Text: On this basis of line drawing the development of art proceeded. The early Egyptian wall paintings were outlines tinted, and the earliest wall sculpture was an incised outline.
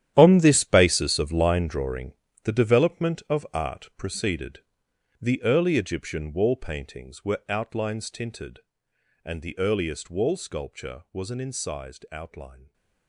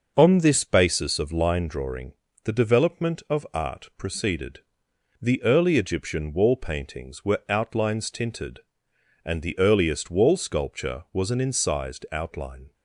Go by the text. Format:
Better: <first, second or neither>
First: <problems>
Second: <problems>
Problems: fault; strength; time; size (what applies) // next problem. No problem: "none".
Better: second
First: gets quieter; strong; throughout; 15 dB // starts louder than the rest; strong; until 1.1 s; 11 dB // pauses between "drawing" and "the"; slight; at 2.1 s; 0.30 s long // stays silent after the last word; slight; from 12.5 s on; 0.5 s long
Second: starts louder than the rest; noticeable; until 1.1 s; 6 dB // pauses between "drawing" and "the"; slight; at 2.1 s; 0.30 s long